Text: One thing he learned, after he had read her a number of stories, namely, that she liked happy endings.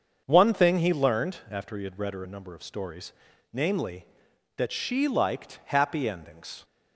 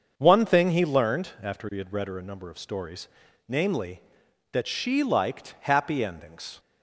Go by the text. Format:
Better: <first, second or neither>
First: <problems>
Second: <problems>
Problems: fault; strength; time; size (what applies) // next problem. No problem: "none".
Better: neither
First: starts louder than the rest; until 1.2 s; 6.5 dB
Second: starts louder than the rest; until 1.1 s; 6.5 dB